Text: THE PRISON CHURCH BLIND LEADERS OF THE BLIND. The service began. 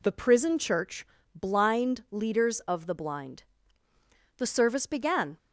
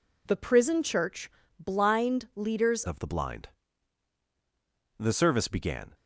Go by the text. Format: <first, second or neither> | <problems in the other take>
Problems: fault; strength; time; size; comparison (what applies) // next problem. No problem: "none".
first | pauses between "CHURCH" and "BLIND"; slight; at 1.3 s; 0.30 s long; slight in the first // changes voice at "OF"; from 2.8 s on; 3.1 s long